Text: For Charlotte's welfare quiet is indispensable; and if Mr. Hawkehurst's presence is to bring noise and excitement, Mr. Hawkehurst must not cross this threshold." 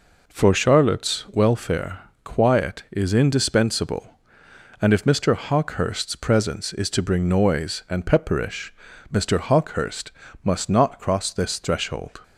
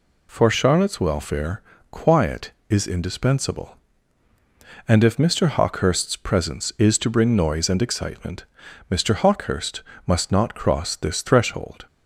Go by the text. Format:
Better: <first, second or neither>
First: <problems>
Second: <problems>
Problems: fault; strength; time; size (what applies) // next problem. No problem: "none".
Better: second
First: pauses between "welfare" and "quiet"; slight; at 1.9 s; 0.24 s long // says "pepperish" for "excitement"; at 8.0 s // pauses between "Hawkehurst" and "must"; slight; at 10.0 s; 0.34 s long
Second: pauses between "welfare" and "quiet"; slight; at 1.5 s; 0.30 s long // pauses between "Hawkehurst" and "must"; slight; at 9.8 s; 0.24 s long